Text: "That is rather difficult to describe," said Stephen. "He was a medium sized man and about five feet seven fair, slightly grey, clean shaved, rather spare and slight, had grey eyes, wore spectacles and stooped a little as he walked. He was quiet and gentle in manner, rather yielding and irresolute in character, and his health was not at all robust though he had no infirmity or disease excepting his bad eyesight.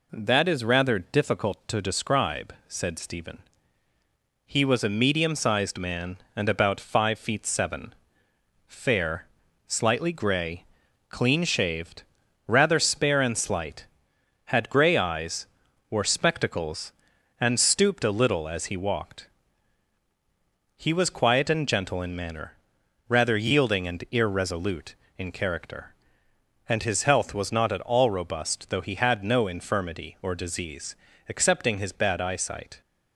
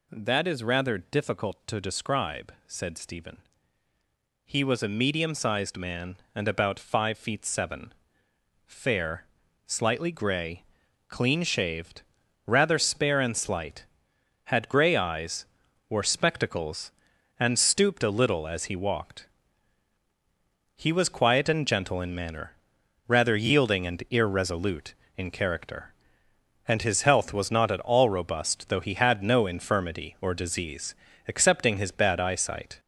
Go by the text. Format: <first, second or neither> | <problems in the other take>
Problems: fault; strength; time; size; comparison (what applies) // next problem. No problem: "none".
first | gets louder; noticeable; throughout; 5 dB // pauses between "seven" and "fair"; noticeable; at 7.9 s; 0.72 s long; noticeable in the first // pauses between "disease" and "excepting"; slight; at 30.9 s; 0.34 s long; slight in the first